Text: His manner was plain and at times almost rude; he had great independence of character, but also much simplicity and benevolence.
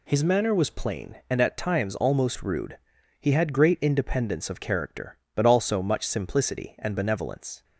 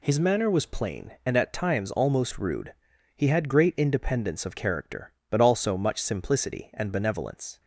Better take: neither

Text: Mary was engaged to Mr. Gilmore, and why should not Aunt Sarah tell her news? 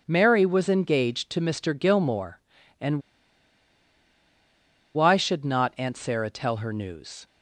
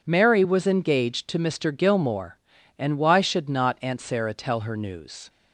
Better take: second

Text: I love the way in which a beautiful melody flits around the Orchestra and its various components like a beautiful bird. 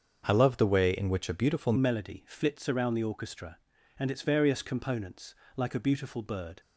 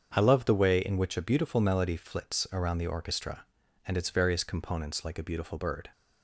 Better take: second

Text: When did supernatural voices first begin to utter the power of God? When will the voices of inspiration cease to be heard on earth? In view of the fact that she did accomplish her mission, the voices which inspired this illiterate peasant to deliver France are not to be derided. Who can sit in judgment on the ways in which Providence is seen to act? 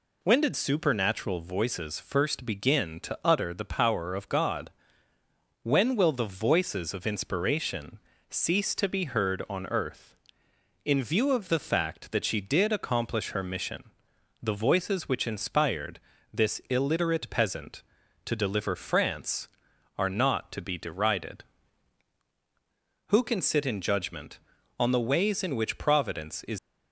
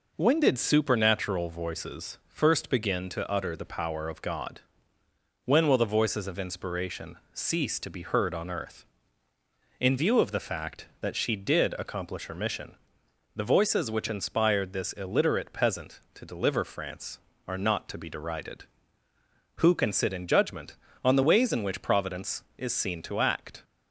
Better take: second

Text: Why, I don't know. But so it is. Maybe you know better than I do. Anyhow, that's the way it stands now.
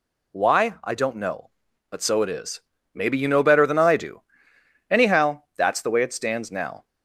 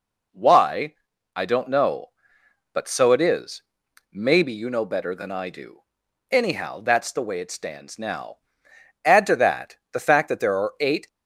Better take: first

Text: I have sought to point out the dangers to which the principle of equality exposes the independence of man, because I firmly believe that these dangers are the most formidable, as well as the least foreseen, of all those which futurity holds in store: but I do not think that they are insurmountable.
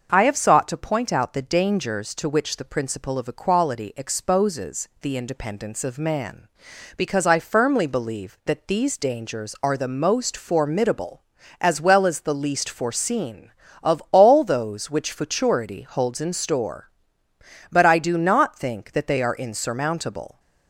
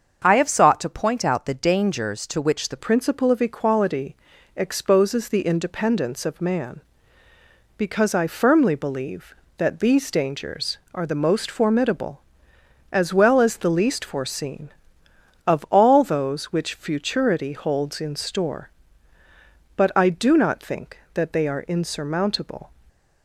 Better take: first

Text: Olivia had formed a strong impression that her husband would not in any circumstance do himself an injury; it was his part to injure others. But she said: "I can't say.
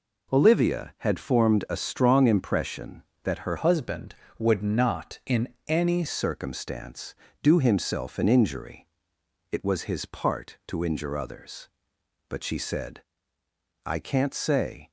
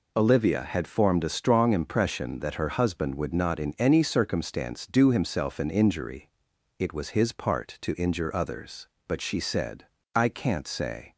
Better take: second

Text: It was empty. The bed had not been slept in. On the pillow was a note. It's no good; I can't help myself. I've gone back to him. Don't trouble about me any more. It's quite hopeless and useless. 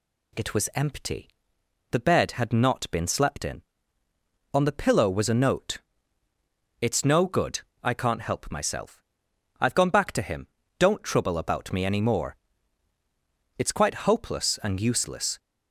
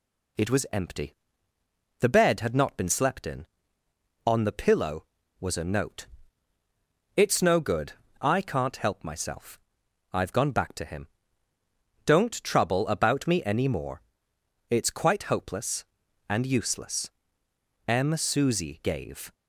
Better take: first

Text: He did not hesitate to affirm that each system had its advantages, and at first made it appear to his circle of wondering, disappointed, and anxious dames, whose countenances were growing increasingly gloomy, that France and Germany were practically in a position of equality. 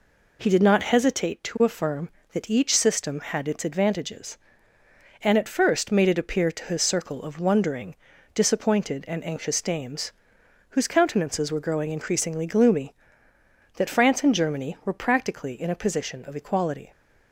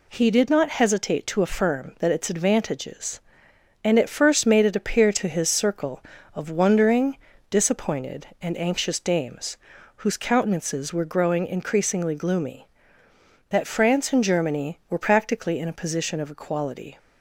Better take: first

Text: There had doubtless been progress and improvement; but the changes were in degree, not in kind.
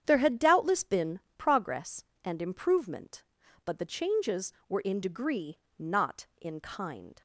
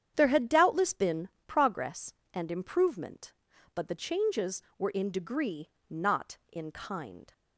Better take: neither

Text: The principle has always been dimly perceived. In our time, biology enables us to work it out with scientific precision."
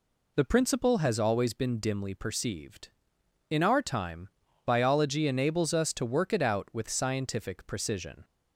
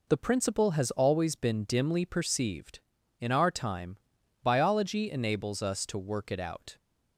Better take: first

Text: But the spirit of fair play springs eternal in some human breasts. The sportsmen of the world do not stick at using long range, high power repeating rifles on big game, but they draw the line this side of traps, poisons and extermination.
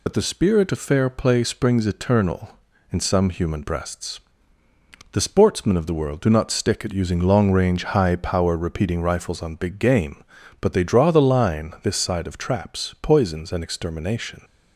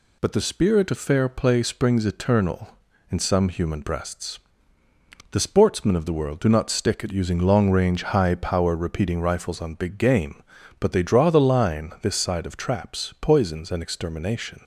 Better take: second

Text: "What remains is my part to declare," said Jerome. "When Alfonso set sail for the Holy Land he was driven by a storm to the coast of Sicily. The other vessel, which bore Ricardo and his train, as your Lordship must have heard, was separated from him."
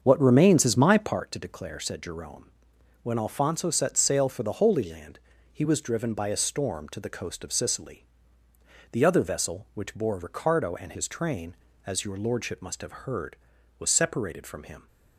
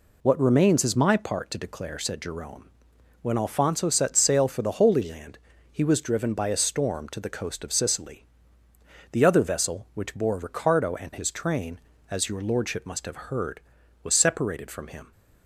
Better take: second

